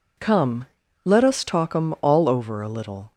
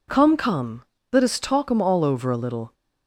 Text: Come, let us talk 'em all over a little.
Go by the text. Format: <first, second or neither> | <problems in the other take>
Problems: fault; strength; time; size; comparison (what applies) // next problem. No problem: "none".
first | says "Come" twice; at 0.3 s